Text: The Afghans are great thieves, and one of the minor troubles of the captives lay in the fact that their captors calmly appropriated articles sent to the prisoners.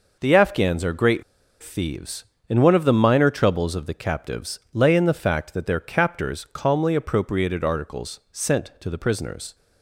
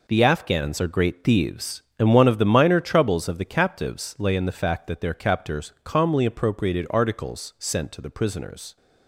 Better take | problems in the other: second | pauses between "great" and "thieves"; at 1.2 s; 0.39 s long

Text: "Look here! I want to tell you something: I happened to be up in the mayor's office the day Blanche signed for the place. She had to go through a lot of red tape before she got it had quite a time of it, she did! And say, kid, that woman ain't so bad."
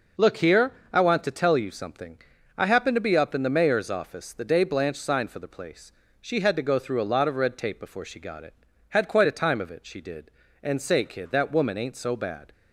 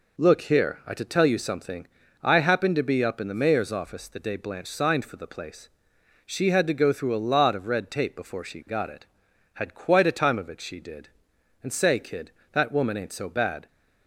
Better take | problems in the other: first | skips "want"; at 0.9 s

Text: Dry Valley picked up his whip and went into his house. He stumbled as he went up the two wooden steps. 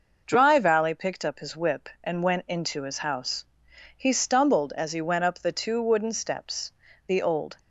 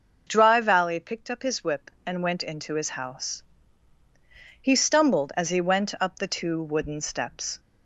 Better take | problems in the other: second | goes on to say "The old"; from 7.0 s on; 0.50 s long

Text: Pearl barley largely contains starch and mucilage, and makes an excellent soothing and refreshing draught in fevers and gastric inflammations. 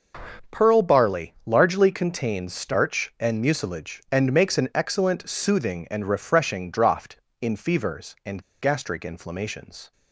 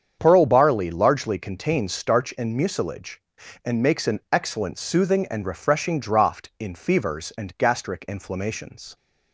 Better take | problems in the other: second | starts louder than the rest; until 1.6 s; 6.5 dB; strong in the second // pauses between "and" and "gastric"; slight; at 8.4 s; 0.19 s long

